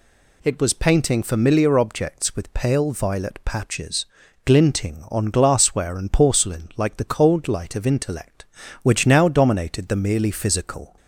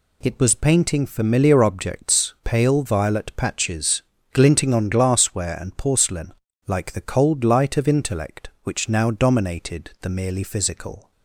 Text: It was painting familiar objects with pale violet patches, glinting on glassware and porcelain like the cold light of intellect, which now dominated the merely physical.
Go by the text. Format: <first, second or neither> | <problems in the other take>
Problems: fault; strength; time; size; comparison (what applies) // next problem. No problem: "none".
first | skips "with"; at 2.3 s // pauses between "porcelain" and "like"; slight; at 6.3 s; 0.34 s long